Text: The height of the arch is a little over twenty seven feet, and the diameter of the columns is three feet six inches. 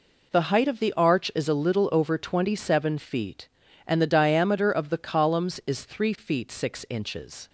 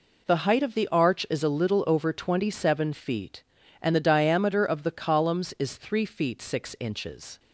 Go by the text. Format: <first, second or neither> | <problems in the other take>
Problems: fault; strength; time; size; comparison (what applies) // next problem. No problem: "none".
neither | none